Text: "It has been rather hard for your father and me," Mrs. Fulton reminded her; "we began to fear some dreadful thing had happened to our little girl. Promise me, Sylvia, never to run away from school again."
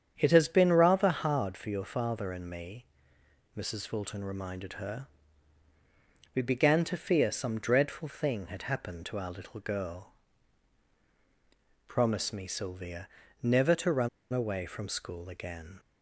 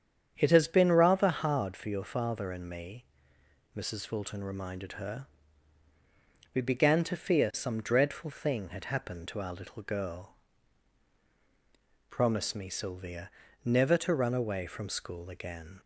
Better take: second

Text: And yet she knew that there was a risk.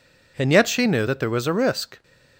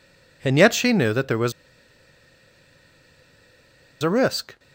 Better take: first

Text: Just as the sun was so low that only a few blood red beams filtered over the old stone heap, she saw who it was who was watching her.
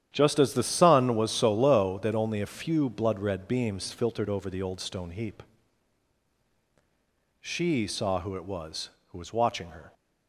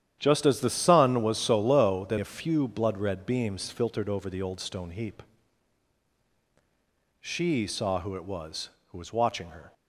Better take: first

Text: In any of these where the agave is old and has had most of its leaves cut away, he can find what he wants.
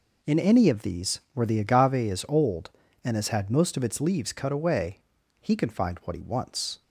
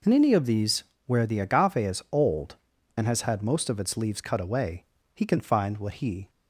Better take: first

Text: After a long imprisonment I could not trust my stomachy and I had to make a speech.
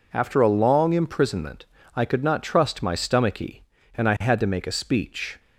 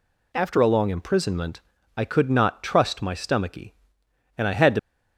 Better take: first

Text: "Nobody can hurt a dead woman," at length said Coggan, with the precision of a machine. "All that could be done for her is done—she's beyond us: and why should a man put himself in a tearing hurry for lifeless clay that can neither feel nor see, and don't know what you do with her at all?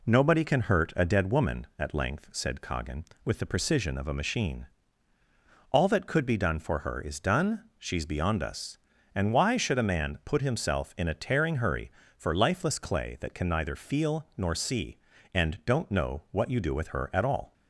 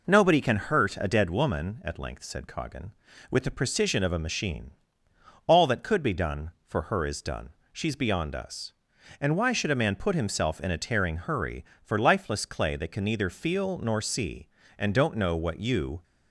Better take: first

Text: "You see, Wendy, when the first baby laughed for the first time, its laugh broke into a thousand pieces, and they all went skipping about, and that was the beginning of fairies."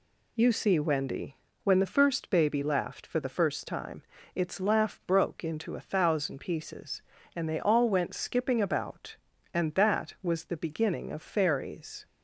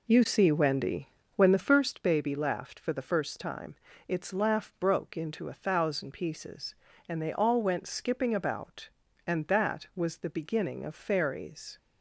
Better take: first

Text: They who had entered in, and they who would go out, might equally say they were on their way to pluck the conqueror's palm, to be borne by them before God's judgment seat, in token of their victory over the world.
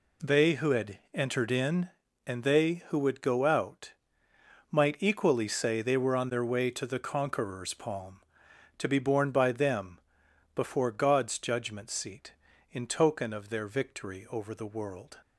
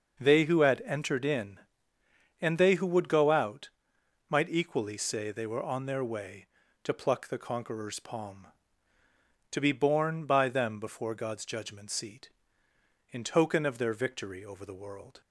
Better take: second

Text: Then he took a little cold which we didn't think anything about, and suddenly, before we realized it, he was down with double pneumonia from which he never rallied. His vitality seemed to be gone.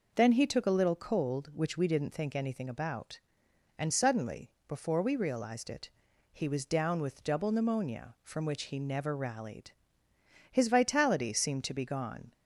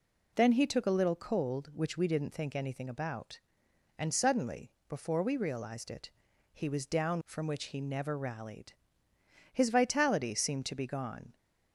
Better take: first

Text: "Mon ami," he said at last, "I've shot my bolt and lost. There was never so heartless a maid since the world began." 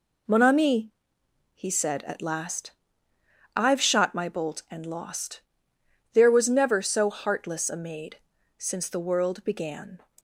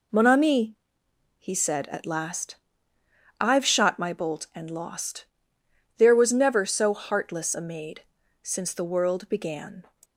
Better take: neither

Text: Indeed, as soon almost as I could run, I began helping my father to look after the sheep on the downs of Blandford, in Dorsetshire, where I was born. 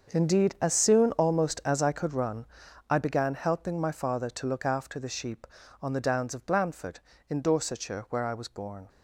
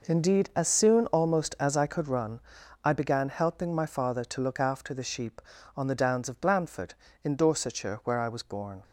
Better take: second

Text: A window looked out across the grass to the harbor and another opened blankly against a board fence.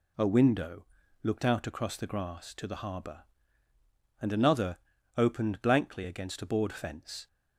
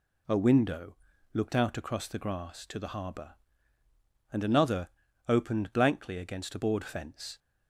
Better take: neither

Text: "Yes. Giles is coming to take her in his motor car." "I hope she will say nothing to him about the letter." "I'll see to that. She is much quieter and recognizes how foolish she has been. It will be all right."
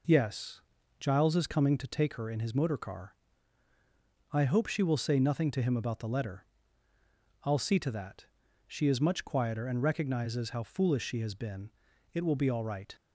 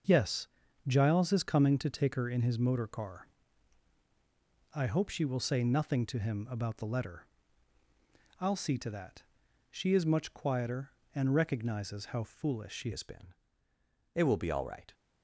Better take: first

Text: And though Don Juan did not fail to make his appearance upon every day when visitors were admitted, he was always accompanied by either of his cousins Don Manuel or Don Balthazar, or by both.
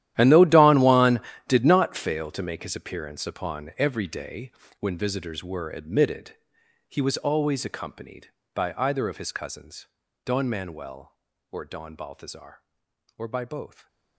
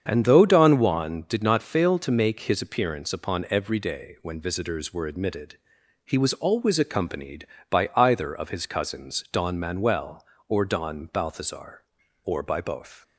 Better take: second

